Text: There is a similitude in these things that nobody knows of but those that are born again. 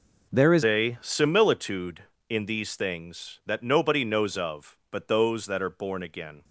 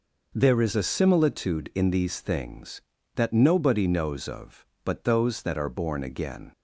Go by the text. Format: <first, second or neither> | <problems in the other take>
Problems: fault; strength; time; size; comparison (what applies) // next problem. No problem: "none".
second | changes voice at "a"; from 0.6 s on; 5.8 s long